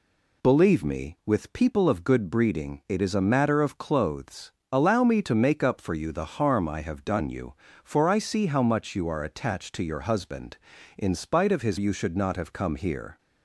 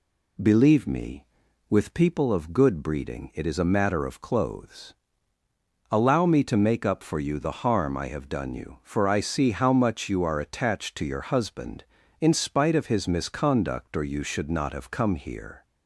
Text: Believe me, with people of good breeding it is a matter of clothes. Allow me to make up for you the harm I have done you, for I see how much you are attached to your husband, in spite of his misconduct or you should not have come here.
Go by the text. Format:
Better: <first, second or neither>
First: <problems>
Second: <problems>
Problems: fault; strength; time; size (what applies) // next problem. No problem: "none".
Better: second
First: skips "misconduct or"; at 11.7 s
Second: none